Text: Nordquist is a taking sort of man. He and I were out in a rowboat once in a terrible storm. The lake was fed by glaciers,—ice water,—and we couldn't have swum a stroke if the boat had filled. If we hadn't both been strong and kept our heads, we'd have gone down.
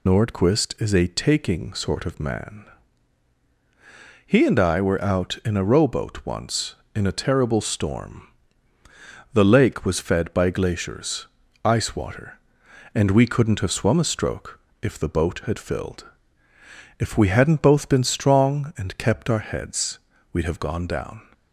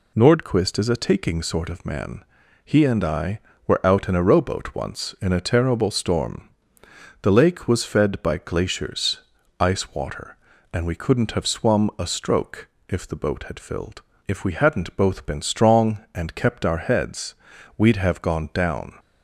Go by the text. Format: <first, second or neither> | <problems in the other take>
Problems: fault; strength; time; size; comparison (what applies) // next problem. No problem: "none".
second | loses the start of "Nordquist"; at 0.0 s; 70 ms // pauses between "stroke" and "if"; slight; at 14.5 s; 0.24 s long; slight in the second